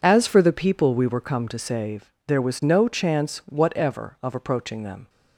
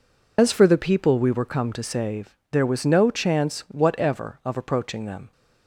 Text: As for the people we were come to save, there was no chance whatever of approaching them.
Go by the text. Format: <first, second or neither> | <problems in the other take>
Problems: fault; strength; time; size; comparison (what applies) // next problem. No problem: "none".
first | loses the start of "As"; at 0.3 s; 105 ms